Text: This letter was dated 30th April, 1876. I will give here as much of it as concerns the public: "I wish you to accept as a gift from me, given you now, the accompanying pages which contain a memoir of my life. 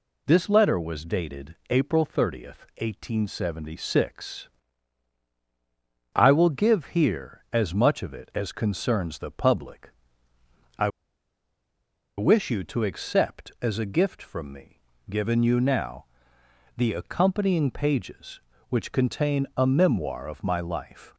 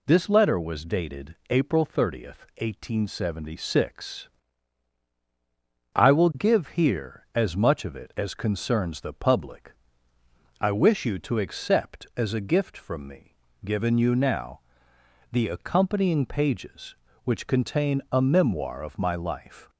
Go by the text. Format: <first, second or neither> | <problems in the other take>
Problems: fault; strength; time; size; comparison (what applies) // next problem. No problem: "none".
second | pauses between "I" and "wish"; strong; at 10.8 s; 1.2 s long